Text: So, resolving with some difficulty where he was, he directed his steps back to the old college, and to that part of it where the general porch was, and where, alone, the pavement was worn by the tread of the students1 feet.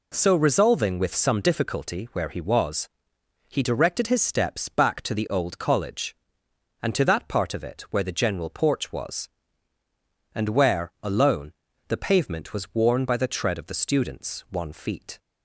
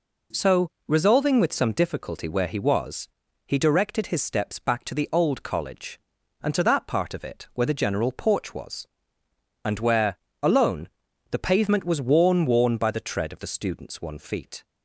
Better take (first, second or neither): first